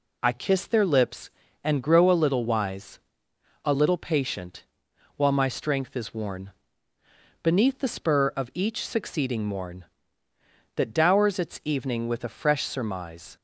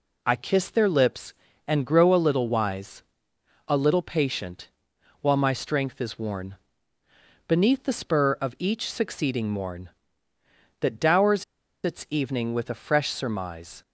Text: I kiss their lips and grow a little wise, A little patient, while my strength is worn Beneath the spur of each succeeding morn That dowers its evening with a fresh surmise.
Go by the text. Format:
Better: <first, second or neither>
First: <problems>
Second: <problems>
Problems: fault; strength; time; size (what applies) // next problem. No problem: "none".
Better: first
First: pauses between "worn" and "Beneath"; noticeable; at 6.5 s; 0.90 s long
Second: pauses between "worn" and "Beneath"; noticeable; at 6.5 s; 0.90 s long // pauses between "dowers" and "its"; at 11.4 s; 0.40 s long